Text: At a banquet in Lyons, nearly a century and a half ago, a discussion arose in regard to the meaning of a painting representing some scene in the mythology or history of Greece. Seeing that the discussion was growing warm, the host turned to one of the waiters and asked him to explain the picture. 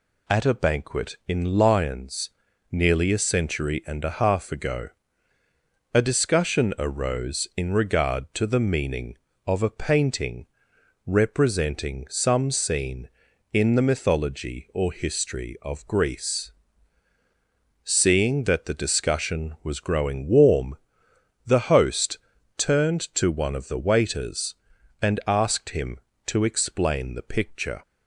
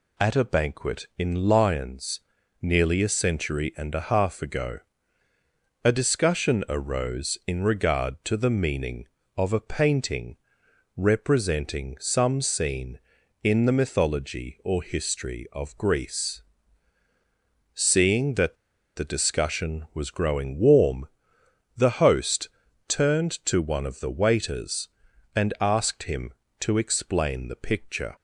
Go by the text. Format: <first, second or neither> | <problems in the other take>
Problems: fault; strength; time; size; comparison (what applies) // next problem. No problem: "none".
first | pauses between "painting" and "representing"; noticeable; at 10.3 s; 0.58 s long; noticeable in the first // pauses between "that" and "the"; at 18.5 s; 0.41 s long // pauses between "host" and "turned"; at 22.4 s; 0.40 s long; also in the first